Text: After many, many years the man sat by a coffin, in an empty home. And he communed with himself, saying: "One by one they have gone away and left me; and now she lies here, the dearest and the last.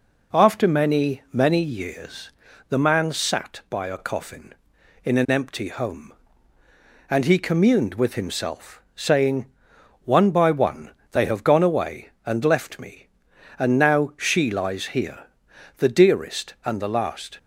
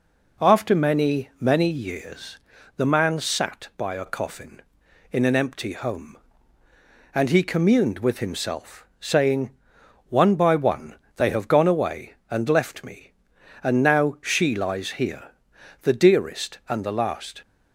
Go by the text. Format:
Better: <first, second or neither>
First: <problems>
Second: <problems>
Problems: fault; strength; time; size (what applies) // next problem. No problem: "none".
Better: neither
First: pauses between "years" and "the"; at 2.2 s; 0.38 s long // pauses between "one" and "they"; slight; at 10.8 s; 0.22 s long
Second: pauses between "years" and "the"; at 2.3 s; 0.38 s long // pauses between "one" and "they"; slight; at 10.9 s; 0.22 s long